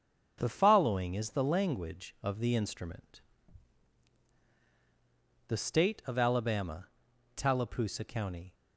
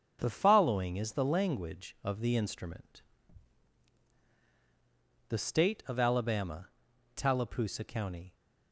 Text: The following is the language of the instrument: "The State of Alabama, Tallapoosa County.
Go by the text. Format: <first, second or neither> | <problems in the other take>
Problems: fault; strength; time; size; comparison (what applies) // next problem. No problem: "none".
neither | starts louder than the rest; noticeable; the same in both